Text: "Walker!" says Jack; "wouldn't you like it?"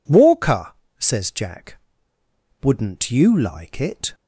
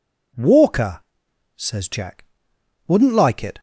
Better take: first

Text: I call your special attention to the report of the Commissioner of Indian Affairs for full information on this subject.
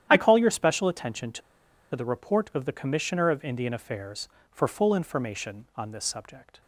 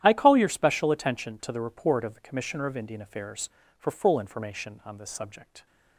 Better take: second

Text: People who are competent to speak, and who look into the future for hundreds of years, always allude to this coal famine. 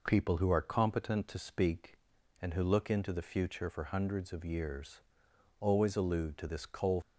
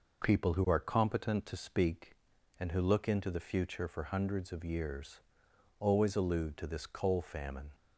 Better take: second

